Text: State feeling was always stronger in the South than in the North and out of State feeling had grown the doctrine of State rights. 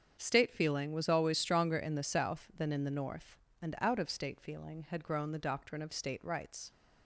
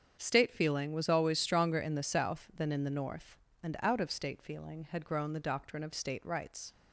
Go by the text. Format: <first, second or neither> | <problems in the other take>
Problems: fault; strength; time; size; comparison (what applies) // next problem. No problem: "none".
neither | starts louder than the rest; strong; the same in both